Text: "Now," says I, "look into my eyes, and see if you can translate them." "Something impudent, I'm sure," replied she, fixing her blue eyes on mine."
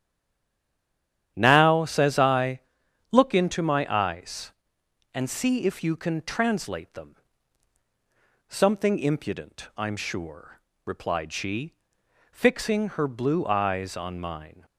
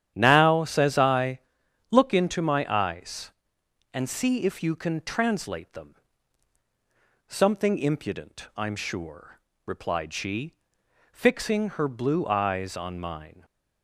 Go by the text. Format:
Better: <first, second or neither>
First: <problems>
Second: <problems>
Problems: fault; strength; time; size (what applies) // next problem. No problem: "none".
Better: second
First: stays silent before the first word; noticeable; until 1.3 s; 1.3 s long // starts louder than the rest; strong; until 2.3 s; 10 dB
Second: starts louder than the rest; strong; until 1.1 s; 10 dB